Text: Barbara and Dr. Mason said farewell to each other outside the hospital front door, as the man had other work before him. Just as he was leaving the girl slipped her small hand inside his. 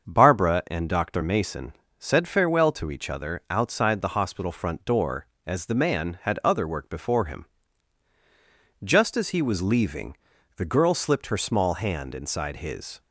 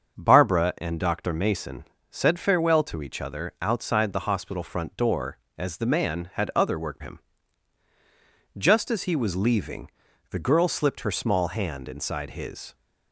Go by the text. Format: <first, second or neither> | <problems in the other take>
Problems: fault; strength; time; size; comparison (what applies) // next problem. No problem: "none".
first | starts louder than the rest; until 1.2 s; 6.5 dB; also in the first // pauses between "Mason" and "said"; slight; at 1.8 s; 0.26 s long; slight in the first // skips "before"; at 7.0 s // pauses between "leaving" and "the"; at 9.8 s; 0.42 s long; also in the first